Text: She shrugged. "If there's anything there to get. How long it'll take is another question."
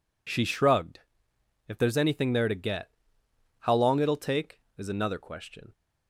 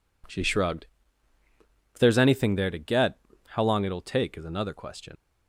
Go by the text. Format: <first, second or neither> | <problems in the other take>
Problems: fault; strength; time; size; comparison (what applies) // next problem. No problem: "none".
first | leaves "question" unfinished; at 5.1 s; 95 ms